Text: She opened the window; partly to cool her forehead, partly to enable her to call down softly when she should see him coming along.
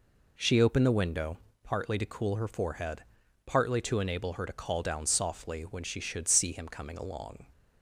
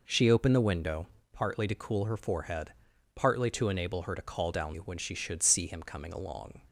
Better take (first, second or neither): first